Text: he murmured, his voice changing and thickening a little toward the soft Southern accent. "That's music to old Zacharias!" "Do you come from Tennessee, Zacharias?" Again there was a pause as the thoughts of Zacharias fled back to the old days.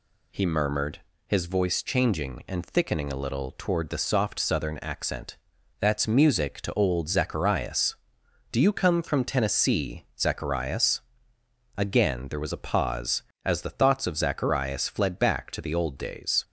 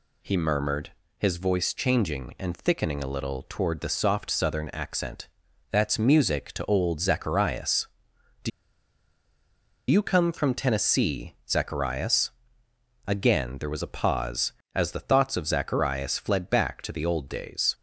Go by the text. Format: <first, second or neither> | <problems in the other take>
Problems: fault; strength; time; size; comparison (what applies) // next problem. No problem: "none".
first | pauses between "Do" and "you"; strong; at 8.5 s; 1.4 s long